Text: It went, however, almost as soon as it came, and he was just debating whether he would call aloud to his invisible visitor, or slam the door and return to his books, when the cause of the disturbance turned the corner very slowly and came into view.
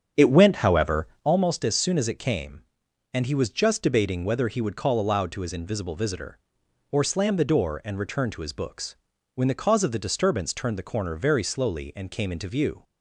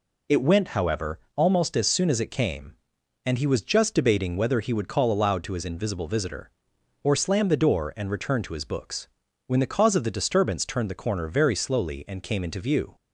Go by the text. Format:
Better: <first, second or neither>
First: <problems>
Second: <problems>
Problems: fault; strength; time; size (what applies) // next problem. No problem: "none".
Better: second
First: starts louder than the rest; strong; until 1.3 s; 7.5 dB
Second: none